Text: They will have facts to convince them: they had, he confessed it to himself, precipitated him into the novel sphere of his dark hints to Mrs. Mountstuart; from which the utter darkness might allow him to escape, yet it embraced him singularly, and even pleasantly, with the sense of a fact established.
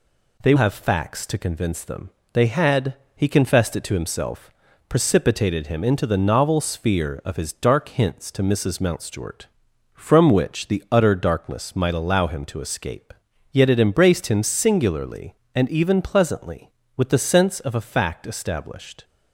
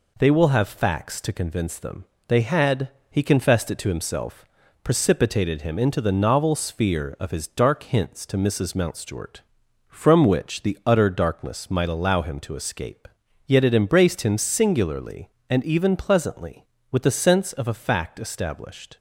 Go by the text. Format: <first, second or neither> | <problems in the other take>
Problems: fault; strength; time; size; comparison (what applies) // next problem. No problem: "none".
second | skips "will"; at 0.5 s